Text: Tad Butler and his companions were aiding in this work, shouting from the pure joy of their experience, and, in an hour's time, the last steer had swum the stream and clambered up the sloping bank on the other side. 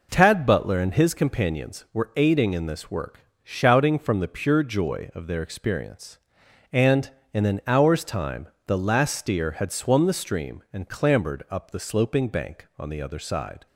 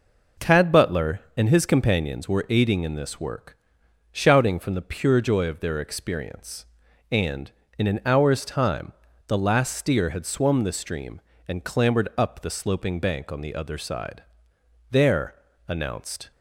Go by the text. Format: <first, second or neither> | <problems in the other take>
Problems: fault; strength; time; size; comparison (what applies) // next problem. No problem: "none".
first | goes on to say "There announced"; from 14.9 s on; 1.4 s long